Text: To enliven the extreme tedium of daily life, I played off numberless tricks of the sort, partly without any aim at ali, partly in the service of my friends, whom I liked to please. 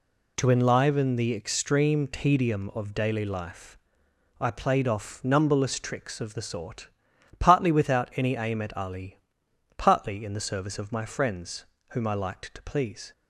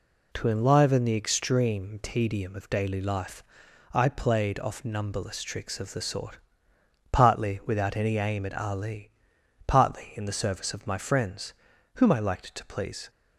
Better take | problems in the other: neither | none

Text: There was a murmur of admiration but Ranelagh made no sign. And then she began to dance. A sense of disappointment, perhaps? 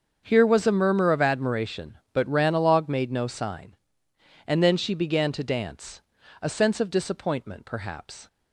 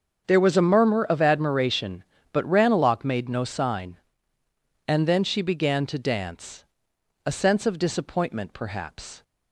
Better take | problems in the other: second | starts louder than the rest; until 1.2 s; 7 dB; also in the second // says "Here" for "There"; at 0.2 s

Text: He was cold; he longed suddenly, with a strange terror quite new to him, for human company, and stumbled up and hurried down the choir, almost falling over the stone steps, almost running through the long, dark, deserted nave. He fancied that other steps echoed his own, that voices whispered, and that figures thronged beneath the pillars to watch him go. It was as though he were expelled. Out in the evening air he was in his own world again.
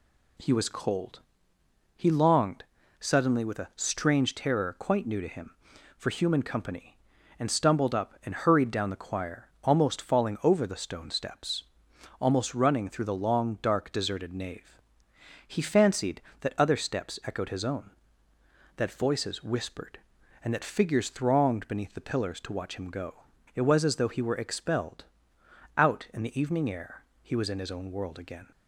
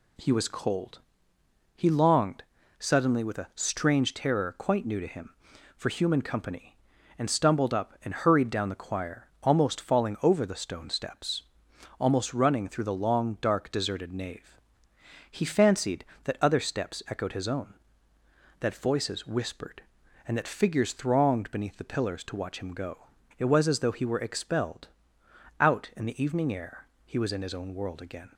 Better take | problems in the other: neither | pauses between "longed" and "suddenly"; slight; the same in both // pauses between "air" and "he"; slight; the same in both

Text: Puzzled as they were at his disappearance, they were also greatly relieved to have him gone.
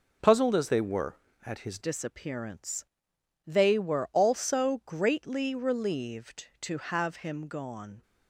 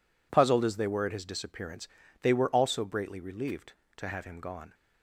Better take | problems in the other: second | changes voice at "disappearance"; from 1.8 s on; 6.2 s long

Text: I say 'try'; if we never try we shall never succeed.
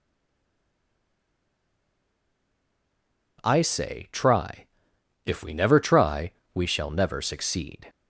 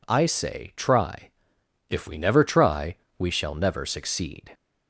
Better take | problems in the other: second | stays silent before the first word; strong; until 3.3 s; 3.3 s long // pauses between "try" and "we"; slight; at 6.3 s; 0.22 s long; slight in the second

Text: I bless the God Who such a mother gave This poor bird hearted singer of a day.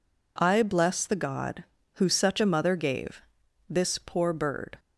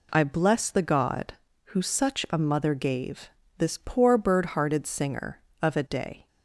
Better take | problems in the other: second | pauses between "gave" and "This"; noticeable; at 3.2 s; 0.48 s long; slight in the second // stops before "hearted singer of a day"; at 4.7 s

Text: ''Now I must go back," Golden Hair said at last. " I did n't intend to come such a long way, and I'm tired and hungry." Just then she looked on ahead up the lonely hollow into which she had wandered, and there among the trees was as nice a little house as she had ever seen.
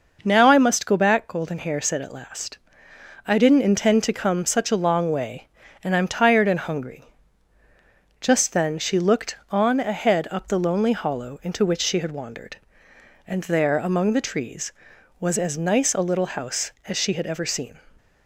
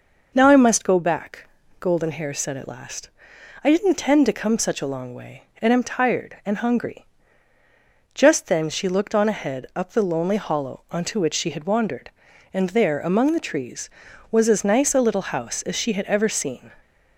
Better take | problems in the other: first | says "onto" for "into"; at 10.9 s

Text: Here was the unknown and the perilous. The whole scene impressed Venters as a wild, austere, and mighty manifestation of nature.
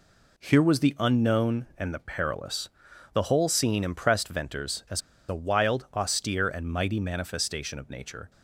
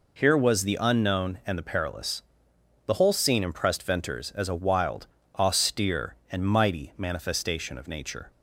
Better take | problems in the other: second | pauses between "as" and "a"; slight; at 5.0 s; 0.28 s long

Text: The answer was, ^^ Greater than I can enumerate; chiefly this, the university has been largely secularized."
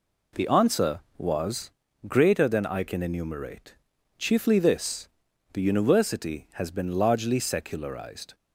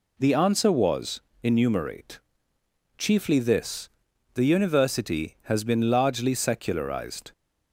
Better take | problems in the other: first | skips "Greater than I can"; at 1.3 s

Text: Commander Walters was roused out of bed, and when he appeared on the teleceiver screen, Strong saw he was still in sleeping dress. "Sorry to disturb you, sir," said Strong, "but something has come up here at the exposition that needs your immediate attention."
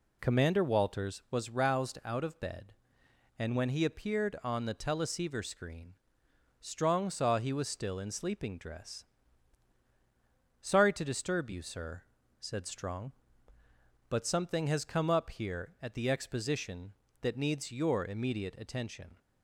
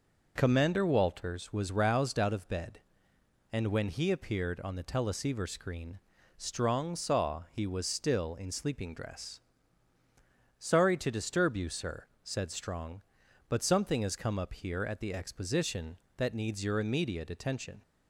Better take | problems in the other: neither | none

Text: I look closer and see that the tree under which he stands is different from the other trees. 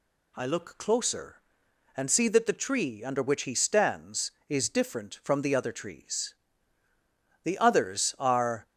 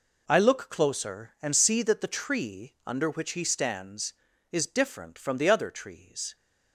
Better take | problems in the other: second | goes on to say "The others are"; noticeable; from 7.4 s on; 1.2 s long

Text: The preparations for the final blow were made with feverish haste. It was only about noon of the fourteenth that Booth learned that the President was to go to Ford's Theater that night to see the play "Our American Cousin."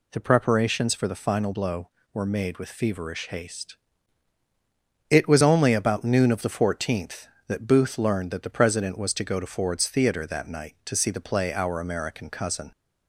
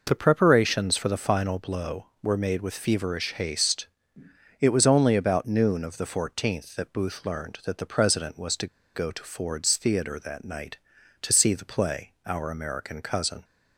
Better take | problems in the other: first | pauses between "to" and "go"; slight; at 8.6 s; 0.28 s long

